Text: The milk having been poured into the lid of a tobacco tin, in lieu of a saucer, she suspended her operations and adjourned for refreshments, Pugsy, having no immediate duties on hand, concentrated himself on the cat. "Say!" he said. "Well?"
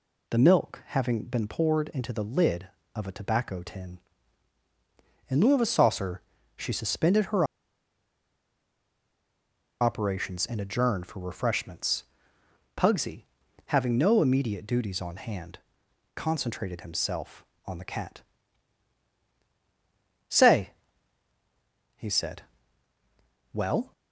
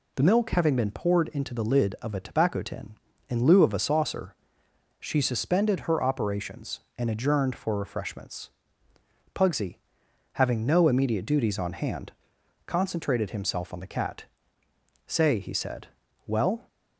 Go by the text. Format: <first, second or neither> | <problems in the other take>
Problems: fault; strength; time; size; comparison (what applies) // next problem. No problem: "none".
second | pauses between "her" and "operations"; strong; at 7.4 s; 2.3 s long